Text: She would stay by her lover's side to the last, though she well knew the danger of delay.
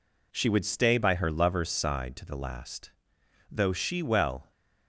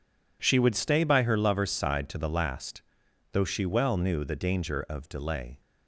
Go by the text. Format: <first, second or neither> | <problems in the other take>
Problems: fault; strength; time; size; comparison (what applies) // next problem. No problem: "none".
second | stops before "knew the danger of delay"; at 4.5 s